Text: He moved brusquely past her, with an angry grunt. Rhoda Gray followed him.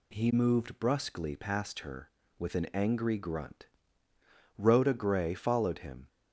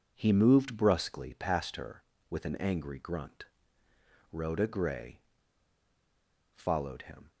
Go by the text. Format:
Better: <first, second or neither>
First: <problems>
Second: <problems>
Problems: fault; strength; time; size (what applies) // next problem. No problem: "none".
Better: first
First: none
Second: pauses between "Gray" and "followed"; strong; at 5.1 s; 1.3 s long